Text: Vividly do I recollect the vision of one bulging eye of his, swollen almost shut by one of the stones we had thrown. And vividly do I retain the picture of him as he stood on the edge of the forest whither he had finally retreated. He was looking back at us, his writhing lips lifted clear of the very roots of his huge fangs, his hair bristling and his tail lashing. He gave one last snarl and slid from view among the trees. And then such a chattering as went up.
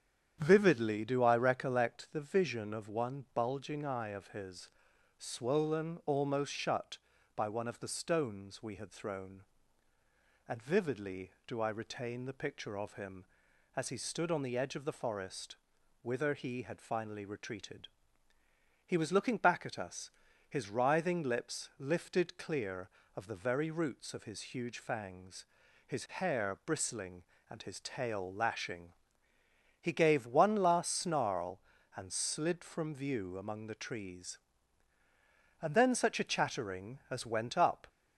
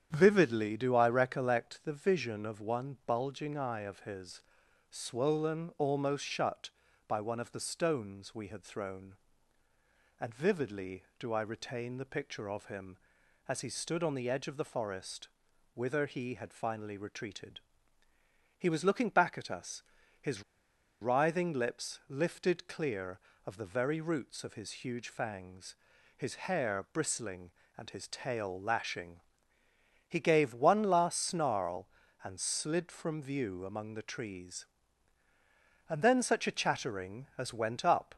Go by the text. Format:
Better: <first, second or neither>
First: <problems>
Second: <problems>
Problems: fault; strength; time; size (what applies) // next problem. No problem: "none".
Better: first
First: starts louder than the rest; strong; until 1.4 s; 9 dB // pauses between "forest" and "whither"; noticeable; at 15.5 s; 0.46 s long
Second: starts louder than the rest; strong; until 1.1 s; 9 dB // pauses between "forest" and "whither"; noticeable; at 15.2 s; 0.46 s long // pauses between "his" and "writhing"; noticeable; at 20.4 s; 0.59 s long